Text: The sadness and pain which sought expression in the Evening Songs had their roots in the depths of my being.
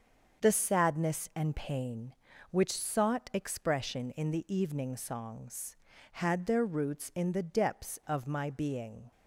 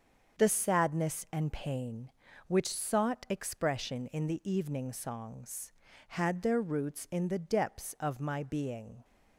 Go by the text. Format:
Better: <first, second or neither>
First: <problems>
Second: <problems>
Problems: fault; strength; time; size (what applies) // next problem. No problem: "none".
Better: neither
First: starts louder than the rest; until 1.4 s; 6.5 dB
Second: starts louder than the rest; until 1.4 s; 6.5 dB